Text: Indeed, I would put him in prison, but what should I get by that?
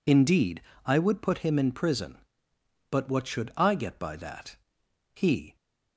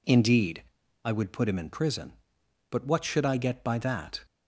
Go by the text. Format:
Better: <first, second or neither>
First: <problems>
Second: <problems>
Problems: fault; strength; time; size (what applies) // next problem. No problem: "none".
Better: second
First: goes on to say "he"; slight; from 5.1 s on; 0.42 s long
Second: none